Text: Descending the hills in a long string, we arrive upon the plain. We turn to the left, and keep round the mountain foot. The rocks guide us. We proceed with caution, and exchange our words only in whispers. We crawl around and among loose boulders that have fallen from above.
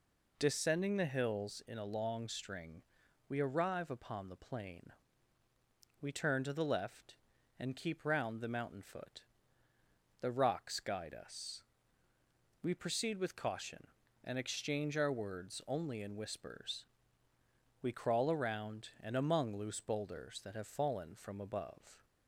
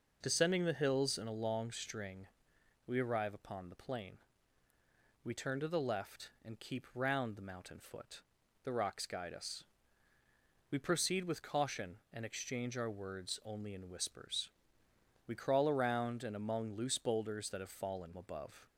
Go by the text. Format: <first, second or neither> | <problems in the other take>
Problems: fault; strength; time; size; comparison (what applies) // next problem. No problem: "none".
first | skips "from"; at 18.1 s